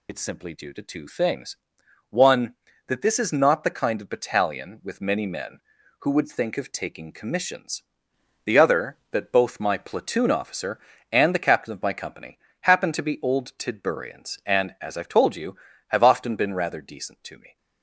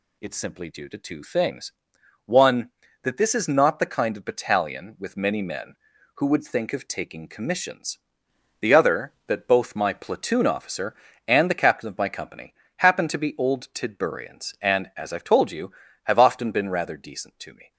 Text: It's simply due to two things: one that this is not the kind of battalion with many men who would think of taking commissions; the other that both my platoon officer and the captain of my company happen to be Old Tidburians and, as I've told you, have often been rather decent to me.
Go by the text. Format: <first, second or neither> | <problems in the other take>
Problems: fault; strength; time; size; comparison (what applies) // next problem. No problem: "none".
second | loses the start of "It's"; at 0.0 s; 45 ms // pauses between "company" and "happen"; slight; at 12.3 s; 0.22 s long; slight in the second